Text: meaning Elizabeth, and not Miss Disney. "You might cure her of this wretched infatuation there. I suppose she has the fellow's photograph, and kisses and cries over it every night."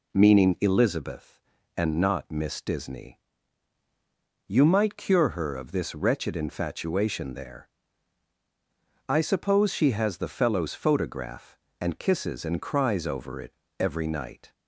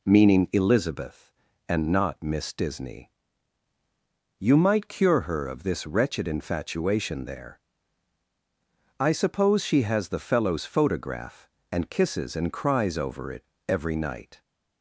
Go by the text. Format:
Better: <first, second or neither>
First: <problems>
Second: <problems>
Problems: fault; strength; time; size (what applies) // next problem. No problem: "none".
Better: neither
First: pauses between "it" and "every"; slight; at 13.5 s; 0.26 s long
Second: pauses between "it" and "every"; slight; at 13.4 s; 0.24 s long